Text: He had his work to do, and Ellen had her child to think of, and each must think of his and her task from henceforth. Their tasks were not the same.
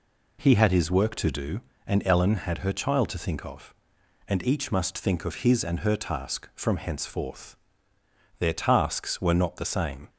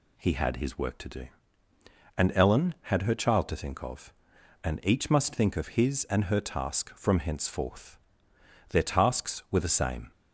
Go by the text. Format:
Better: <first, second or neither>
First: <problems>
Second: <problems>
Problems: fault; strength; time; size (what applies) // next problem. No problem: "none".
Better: first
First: none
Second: skips "not"; at 9.5 s